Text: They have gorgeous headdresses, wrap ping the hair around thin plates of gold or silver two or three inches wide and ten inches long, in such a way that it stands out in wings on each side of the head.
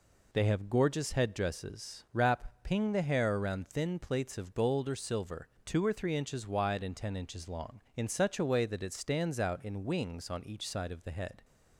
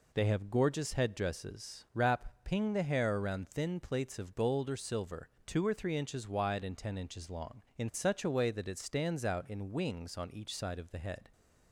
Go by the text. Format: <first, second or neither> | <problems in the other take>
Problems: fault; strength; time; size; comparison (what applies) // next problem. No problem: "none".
neither | pauses between "silver" and "two"; slight; the same in both